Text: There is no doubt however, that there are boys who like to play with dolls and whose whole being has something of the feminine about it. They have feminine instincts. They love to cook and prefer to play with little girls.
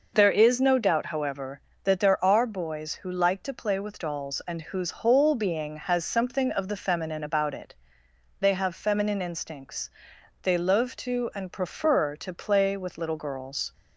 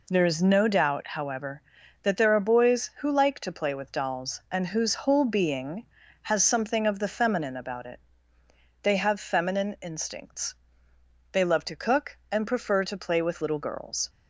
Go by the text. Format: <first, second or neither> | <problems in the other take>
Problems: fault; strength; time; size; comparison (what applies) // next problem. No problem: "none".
second | skips "cook"; at 11.3 s